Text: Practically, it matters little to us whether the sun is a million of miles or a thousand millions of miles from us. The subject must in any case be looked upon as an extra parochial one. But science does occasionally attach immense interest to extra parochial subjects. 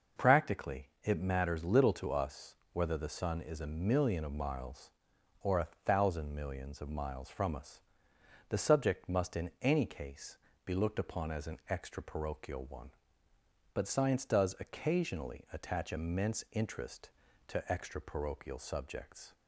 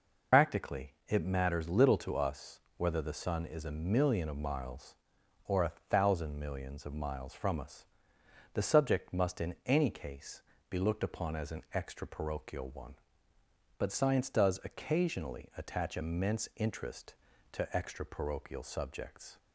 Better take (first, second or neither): first